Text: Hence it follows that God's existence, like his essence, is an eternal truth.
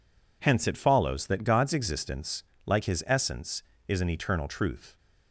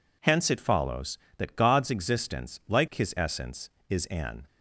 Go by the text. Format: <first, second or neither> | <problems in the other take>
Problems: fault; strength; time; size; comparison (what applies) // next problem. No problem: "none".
first | stops before "eternal truth"; at 4.4 s